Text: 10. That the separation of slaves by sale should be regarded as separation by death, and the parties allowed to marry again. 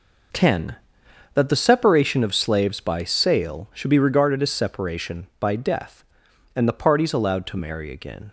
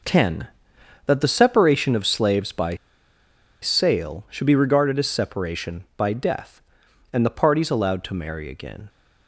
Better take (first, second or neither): first